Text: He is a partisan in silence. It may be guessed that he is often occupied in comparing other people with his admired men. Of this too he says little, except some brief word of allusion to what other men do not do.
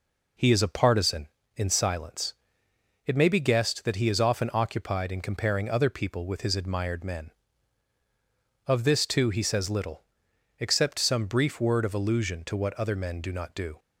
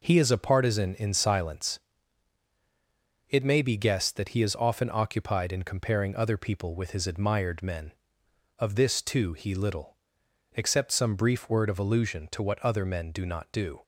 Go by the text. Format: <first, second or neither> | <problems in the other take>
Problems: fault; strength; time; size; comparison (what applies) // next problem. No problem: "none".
first | skips "says"; at 9.5 s